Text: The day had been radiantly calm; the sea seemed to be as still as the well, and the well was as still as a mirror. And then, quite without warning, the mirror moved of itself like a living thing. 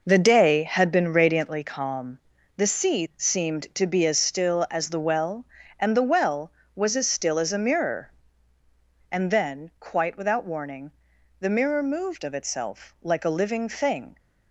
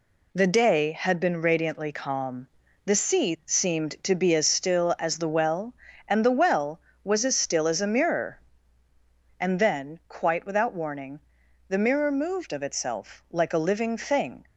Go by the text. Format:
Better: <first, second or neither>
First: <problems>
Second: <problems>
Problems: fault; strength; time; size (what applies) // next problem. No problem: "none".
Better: second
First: starts louder than the rest; noticeable; until 1.6 s; 5.5 dB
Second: none